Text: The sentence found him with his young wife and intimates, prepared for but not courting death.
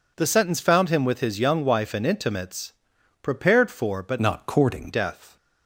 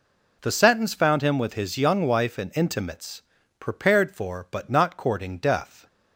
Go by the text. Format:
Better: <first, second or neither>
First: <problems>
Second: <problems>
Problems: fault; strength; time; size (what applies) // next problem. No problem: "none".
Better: second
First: changes voice from "not" to "courting"; from 4.1 to 4.8 s; 0.7 s long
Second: none